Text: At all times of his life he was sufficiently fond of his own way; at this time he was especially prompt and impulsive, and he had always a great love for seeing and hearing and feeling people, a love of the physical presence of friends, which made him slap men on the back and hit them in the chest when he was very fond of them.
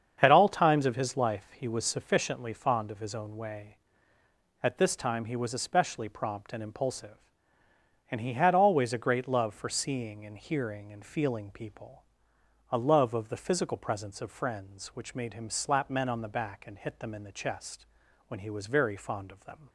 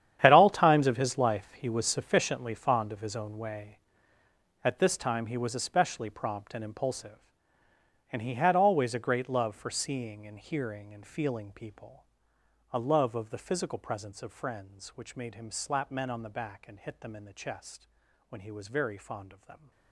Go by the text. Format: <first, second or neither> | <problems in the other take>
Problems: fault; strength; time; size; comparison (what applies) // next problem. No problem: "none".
first | gets quieter; strong; throughout; 16 dB // starts louder than the rest; strong; until 1.2 s; 10 dB; strong in the first // pauses between "chest" and "when"; at 17.8 s; 0.42 s long; also in the first